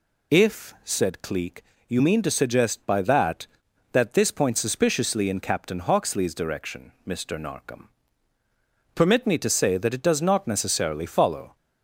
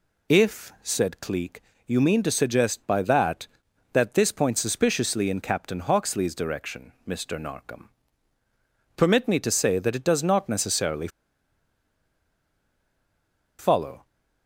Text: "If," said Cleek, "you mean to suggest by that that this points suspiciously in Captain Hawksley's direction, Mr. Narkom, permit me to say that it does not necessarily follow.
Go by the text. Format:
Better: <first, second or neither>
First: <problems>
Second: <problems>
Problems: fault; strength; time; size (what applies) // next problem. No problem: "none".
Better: first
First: none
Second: pauses between "necessarily" and "follow"; strong; at 11.0 s; 2.5 s long